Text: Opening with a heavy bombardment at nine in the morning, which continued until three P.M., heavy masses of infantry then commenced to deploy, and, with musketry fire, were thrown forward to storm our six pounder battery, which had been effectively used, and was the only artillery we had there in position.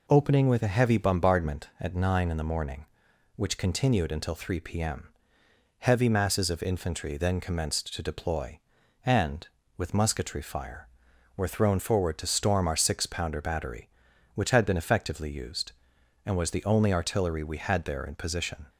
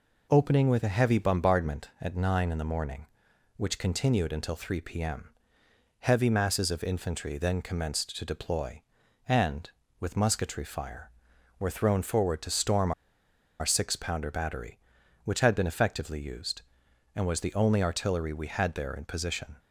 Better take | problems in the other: first | pauses between "storm" and "our"; noticeable; at 12.9 s; 0.68 s long

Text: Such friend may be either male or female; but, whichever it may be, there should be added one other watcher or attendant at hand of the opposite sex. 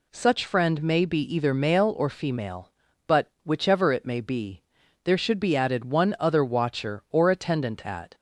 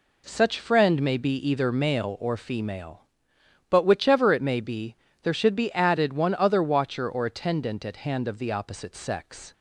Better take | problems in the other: second | stops before "hand of the opposite sex"; at 8.1 s

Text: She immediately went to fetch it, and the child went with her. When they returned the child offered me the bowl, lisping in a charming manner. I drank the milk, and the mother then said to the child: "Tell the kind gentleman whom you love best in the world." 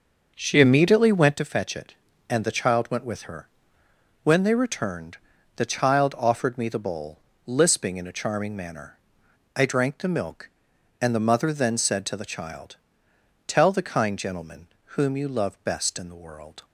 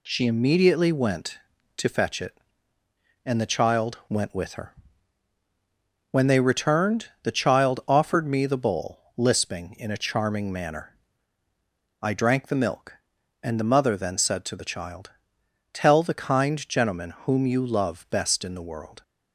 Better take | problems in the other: second | starts louder than the rest; noticeable; until 1.4 s; 6 dB // pauses between "returned" and "the"; at 5.1 s; 0.40 s long; slight in the second // pauses between "gentleman" and "whom"; slight; at 14.6 s; 0.32 s long

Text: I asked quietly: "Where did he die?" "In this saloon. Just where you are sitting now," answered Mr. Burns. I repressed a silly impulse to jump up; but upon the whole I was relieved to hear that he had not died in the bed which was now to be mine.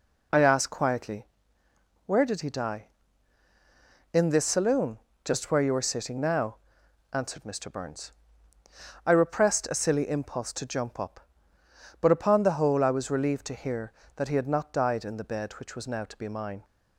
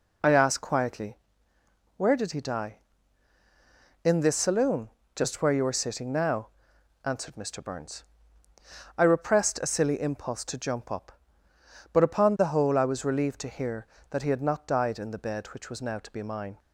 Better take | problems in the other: neither | none

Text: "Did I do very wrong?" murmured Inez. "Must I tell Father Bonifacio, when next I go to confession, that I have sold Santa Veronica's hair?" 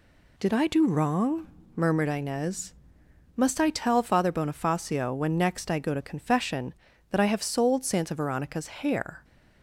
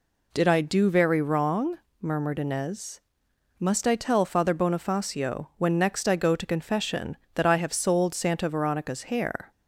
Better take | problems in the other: second | skips "very"; at 0.8 s

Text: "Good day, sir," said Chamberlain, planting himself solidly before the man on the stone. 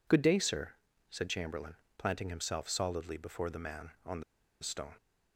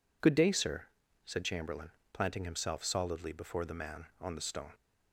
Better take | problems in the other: second | pauses between "the" and "stone"; at 4.2 s; 0.38 s long

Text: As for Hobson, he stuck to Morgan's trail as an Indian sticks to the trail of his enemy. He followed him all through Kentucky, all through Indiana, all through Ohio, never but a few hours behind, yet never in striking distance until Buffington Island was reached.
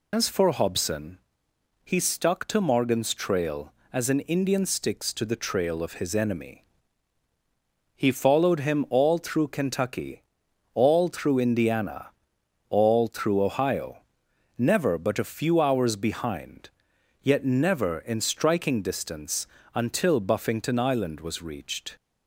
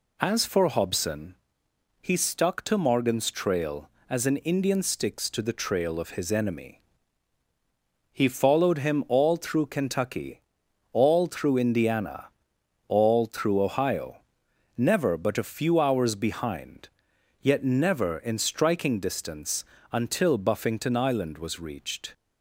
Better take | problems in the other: second | loses the start of "As"; at 0.1 s; 105 ms // pauses between "distance" and "until"; slight; at 19.4 s; 0.26 s long; slight in the second

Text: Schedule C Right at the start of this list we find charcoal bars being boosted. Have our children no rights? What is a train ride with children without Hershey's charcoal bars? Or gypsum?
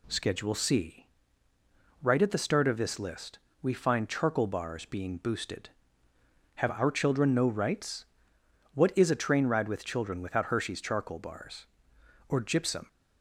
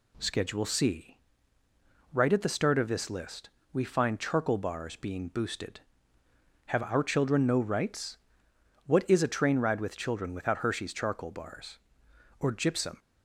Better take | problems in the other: neither | pauses between "C" and "Right"; noticeable; the same in both // pauses between "list" and "we"; slight; the same in both

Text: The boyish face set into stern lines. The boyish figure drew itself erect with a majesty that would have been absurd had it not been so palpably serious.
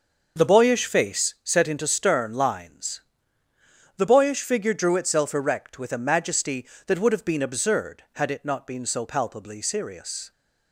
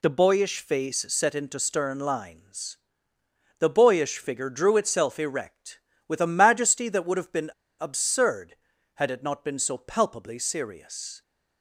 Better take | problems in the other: first | pauses between "been" and "absurd"; slight; at 7.5 s; 0.30 s long

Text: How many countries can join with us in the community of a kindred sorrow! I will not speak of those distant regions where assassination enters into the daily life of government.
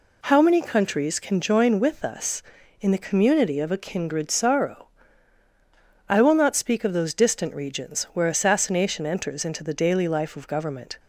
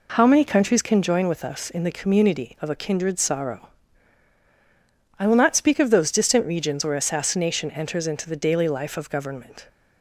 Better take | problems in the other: neither | none

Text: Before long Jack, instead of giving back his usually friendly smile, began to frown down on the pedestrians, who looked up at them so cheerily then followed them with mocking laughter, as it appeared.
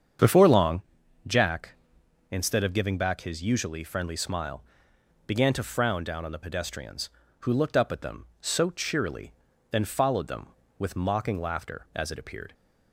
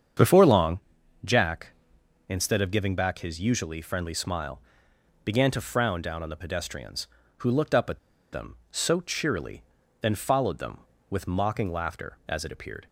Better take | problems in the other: first | starts louder than the rest; strong; until 1.6 s; 7.5 dB; strong in the first // pauses between "long" and "Jack"; at 0.7 s; 0.44 s long; also in the first // pauses between "at" and "them"; slight; at 7.9 s; 0.32 s long // pauses between "cheerily" and "then"; at 9.6 s; 0.38 s long; also in the first

